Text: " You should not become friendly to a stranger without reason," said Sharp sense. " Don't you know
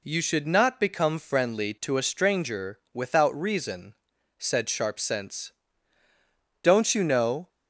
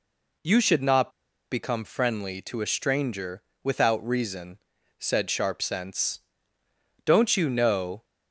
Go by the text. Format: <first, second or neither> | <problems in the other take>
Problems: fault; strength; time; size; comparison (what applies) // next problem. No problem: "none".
first | pauses between "not" and "become"; at 1.0 s; 0.41 s long // pauses between "stranger" and "without"; slight; at 3.4 s; 0.20 s long